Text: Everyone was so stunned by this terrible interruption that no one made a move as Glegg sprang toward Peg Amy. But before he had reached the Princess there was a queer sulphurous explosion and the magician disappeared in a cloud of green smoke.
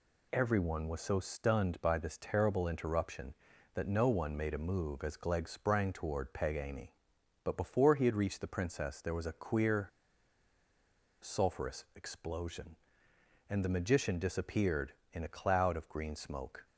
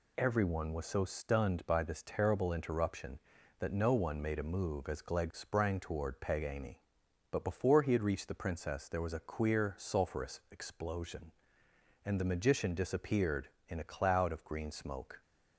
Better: second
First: pauses between "queer" and "sulphurous"; strong; at 9.8 s; 1.3 s long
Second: none

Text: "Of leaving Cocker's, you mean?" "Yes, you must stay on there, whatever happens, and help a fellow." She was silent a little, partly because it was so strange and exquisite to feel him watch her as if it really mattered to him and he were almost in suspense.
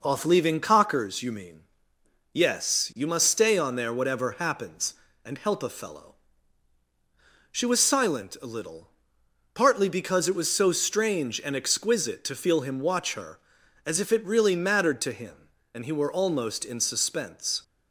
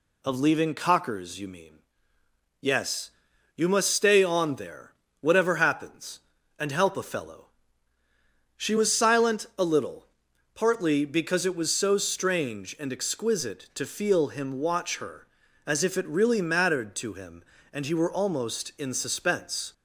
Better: second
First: says "Off" for "Of"; at 0.0 s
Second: none

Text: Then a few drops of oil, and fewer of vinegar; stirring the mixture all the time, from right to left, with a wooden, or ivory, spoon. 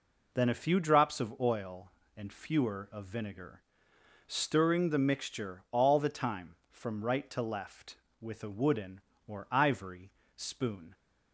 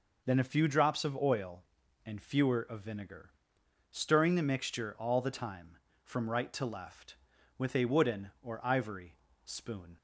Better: neither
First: none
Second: none

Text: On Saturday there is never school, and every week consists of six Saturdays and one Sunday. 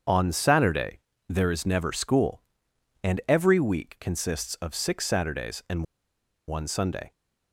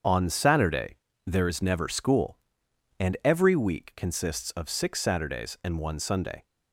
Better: second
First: starts louder than the rest; until 1.3 s; 7 dB // pauses between "Saturday" and "there"; slight; at 1.0 s; 0.28 s long // pauses between "and" and "one"; noticeable; at 5.8 s; 0.63 s long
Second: starts louder than the rest; until 1.3 s; 7 dB // pauses between "Saturday" and "there"; slight; at 0.9 s; 0.28 s long

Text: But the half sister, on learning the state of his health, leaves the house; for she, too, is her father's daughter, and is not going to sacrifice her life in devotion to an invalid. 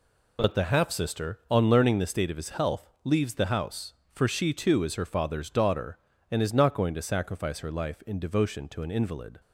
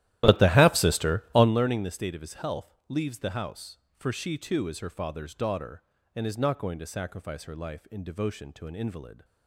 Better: first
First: none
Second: starts louder than the rest; strong; until 1.5 s; 14 dB

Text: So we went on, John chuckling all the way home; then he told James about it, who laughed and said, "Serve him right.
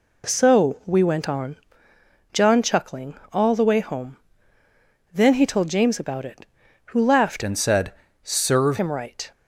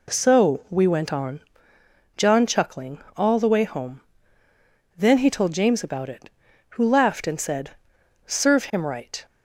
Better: second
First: pauses between "chuckling" and "all"; slight; at 3.1 s; 0.16 s long // changes voice from "and" to "Serve"; from 7.4 to 8.7 s; 1.3 s long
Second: pauses between "chuckling" and "all"; slight; at 2.9 s; 0.16 s long

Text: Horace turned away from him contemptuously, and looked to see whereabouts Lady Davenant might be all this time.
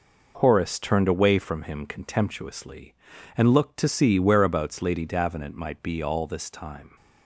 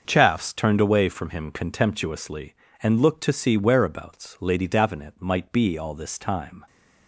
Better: first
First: none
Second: starts louder than the rest; until 1.0 s; 6.5 dB // says "Chaffs" for "Horace"; at 0.0 s

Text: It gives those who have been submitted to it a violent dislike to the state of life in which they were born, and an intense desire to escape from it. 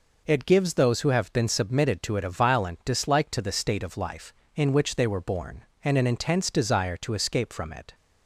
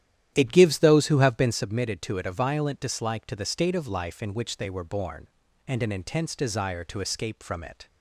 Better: first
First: none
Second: starts louder than the rest; strong; until 1.6 s; 11 dB

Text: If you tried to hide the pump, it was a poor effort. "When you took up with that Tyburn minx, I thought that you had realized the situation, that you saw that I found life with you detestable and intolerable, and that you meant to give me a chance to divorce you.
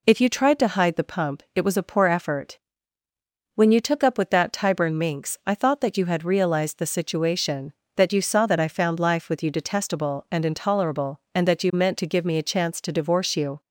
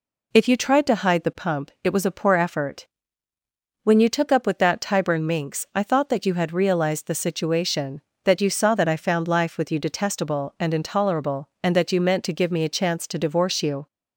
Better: neither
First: none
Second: none

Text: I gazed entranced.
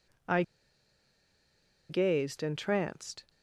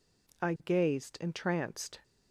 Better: second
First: pauses between "I" and "gazed"; strong; at 0.4 s; 1.4 s long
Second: none

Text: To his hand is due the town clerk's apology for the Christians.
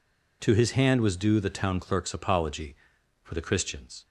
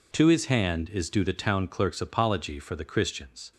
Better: second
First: says "was" for "is"; at 0.9 s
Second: none

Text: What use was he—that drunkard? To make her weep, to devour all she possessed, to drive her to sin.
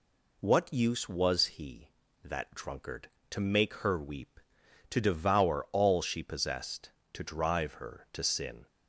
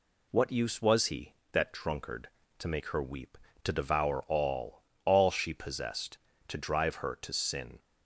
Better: first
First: none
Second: says "all" twice; at 5.0 s

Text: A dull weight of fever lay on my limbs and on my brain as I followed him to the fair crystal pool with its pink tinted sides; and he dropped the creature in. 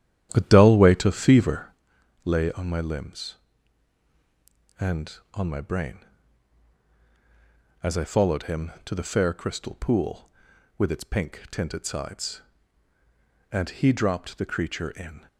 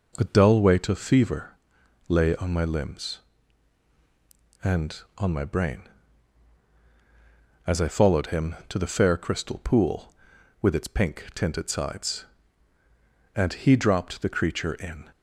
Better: second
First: starts louder than the rest; strong; until 1.8 s; 10.5 dB // pauses between "fever" and "lay"; noticeable; at 1.6 s; 0.54 s long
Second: pauses between "fever" and "lay"; noticeable; at 1.5 s; 0.54 s long

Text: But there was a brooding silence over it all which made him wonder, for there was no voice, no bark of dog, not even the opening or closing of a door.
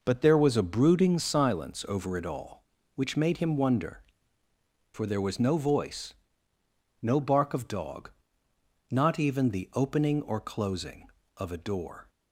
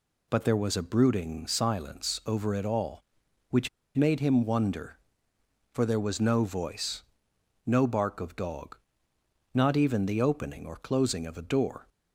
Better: first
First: none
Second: pauses between "which" and "made"; slight; at 3.6 s; 0.27 s long

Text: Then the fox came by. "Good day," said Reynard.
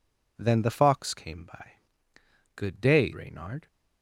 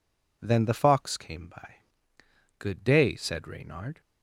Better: second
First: skips "said"; at 3.1 s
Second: none

